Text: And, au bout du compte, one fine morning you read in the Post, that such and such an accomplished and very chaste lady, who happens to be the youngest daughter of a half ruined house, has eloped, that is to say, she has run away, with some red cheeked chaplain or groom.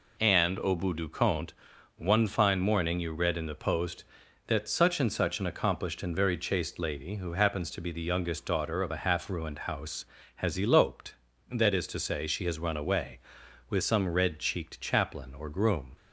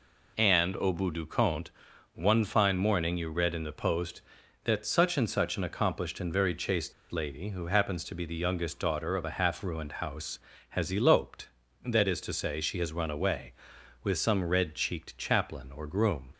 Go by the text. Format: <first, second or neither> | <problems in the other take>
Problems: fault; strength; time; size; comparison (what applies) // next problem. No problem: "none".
first | pauses between "chaste" and "lady"; slight; at 6.9 s; 0.17 s long